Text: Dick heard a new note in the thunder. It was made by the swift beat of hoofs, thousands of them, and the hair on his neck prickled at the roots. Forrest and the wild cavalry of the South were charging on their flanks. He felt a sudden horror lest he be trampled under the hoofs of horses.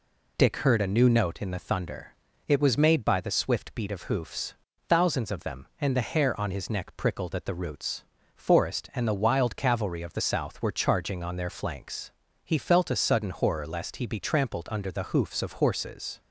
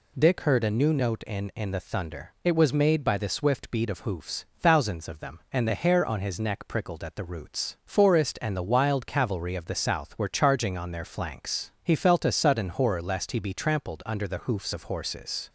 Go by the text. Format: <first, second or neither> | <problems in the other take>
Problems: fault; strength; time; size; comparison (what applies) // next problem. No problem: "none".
first | says "in" twice; at 1.5 s